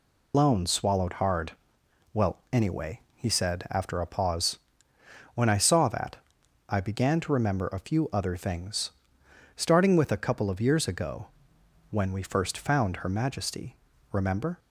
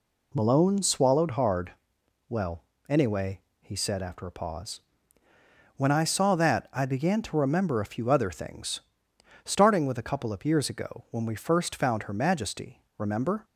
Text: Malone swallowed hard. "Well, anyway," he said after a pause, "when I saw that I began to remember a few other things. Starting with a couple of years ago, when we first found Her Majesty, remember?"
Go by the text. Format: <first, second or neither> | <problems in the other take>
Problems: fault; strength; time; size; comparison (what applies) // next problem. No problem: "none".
second | loses the start of "Malone"; at 0.3 s; 140 ms // pauses between "that" and "I"; noticeable; at 6.1 s; 0.52 s long